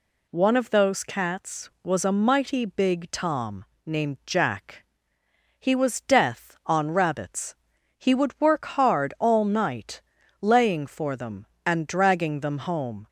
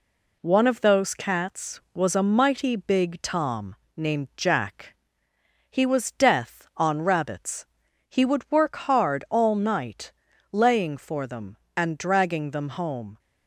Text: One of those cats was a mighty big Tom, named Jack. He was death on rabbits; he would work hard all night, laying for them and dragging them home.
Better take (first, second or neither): first